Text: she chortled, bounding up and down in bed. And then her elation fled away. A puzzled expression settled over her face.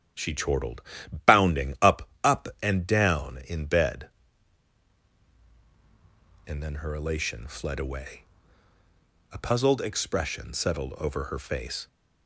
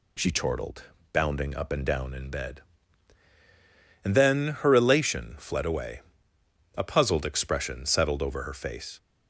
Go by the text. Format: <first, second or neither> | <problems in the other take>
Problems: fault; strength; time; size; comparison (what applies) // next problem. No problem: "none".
second | starts louder than the rest; strong; until 1.5 s; 10 dB // says "up" twice; at 2.2 s